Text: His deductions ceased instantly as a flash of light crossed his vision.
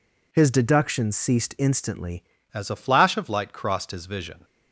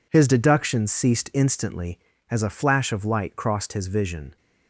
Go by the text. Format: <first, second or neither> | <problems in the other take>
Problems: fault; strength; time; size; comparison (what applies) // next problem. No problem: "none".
second | changes voice at "as"; from 2.5 s on; 1.9 s long